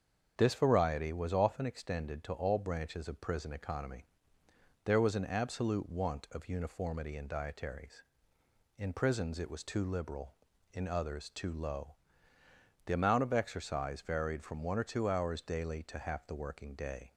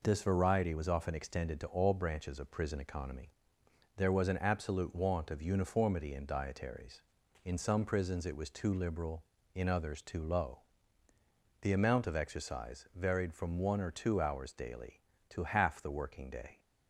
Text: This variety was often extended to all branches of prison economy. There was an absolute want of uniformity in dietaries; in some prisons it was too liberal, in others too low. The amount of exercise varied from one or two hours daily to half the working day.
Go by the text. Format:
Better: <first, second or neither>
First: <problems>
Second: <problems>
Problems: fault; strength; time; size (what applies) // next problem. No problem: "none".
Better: second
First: starts louder than the rest; until 1.3 s; 7 dB // skips "some"; at 8.9 s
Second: none